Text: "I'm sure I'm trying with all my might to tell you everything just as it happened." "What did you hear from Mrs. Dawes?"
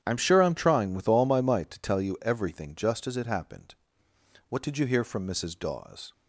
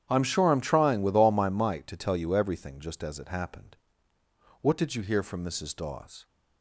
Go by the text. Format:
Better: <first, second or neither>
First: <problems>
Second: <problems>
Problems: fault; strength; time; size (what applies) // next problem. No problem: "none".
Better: neither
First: starts louder than the rest; strong; until 1.0 s; 9.5 dB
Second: starts louder than the rest; strong; until 1.1 s; 10 dB